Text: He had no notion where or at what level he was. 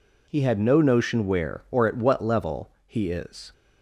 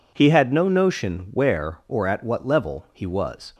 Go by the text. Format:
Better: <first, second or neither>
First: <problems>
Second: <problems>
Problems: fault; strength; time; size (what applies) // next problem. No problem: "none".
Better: second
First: pauses between "level" and "he"; slight; at 2.6 s; 0.18 s long // says "is" for "was"; at 3.0 s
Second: none